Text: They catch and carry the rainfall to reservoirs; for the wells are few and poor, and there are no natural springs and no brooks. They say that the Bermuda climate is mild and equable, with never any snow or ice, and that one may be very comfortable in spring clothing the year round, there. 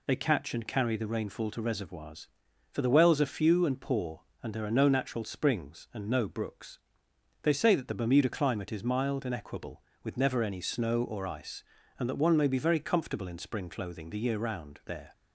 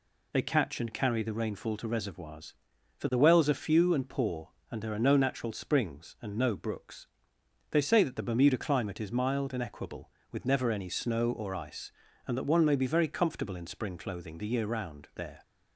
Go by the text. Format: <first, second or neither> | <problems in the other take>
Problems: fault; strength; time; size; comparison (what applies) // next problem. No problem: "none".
neither | none